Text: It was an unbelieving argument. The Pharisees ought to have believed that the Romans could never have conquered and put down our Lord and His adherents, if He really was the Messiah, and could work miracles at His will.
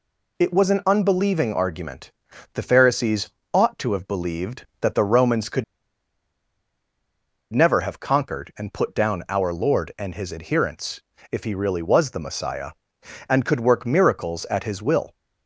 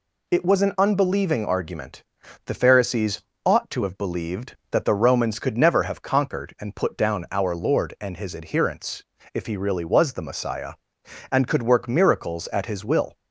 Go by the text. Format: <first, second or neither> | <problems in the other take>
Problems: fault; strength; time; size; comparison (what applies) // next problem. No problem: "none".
second | pauses between "Pharisees" and "ought"; slight; at 3.2 s; 0.24 s long; slight in the second // pauses between "could" and "never"; strong; at 5.6 s; 1.8 s long